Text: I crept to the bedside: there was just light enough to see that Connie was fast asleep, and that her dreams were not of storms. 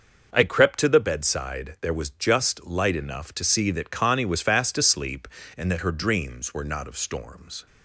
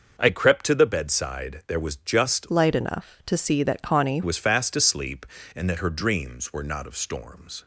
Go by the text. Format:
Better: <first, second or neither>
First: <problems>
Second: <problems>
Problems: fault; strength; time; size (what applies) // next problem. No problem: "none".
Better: first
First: starts louder than the rest; noticeable; until 1.3 s; 6 dB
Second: starts louder than the rest; until 1.2 s; 6 dB // changes voice from "light" to "Connie"; from 2.4 to 4.2 s; 1.8 s long